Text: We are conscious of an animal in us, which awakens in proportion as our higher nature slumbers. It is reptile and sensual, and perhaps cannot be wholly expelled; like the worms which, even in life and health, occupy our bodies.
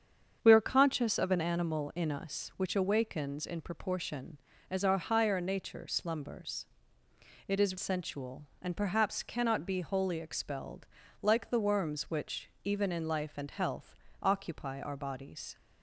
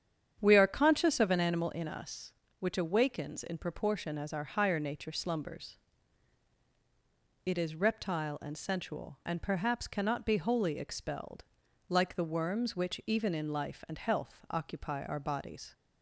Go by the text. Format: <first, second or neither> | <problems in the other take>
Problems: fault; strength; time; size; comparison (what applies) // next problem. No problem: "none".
second | starts louder than the rest; strong; until 1.4 s; 7.5 dB; strong in the second // skips "reptile and"; at 7.7 s